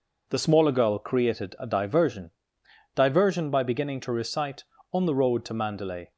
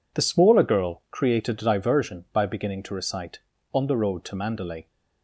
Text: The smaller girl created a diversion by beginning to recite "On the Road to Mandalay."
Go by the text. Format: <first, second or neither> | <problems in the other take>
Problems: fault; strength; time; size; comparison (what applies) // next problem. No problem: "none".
second | says "diversion" twice; at 2.9 s